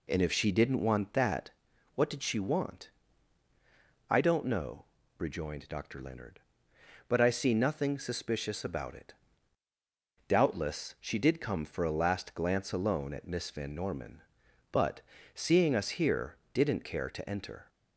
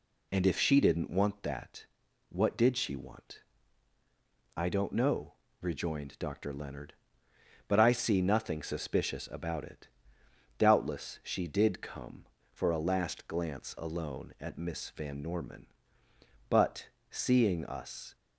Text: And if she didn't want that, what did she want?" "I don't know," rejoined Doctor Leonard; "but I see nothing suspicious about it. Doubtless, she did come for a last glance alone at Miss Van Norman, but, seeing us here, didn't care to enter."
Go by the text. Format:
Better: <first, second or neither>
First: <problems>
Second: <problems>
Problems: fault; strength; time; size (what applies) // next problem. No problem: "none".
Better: first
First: none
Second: stops before "here didn't care to enter"; at 18.1 s